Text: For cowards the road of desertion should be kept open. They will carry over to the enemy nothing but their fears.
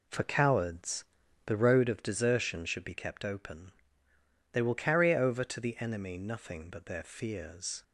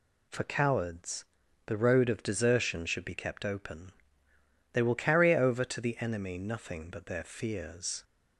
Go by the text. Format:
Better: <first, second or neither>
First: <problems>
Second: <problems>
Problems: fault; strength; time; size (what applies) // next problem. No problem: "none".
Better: second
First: starts louder than the rest; slight; until 1.9 s; 3 dB // pauses between "cowards" and "the"; at 1.0 s; 0.40 s long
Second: pauses between "cowards" and "the"; at 1.2 s; 0.40 s long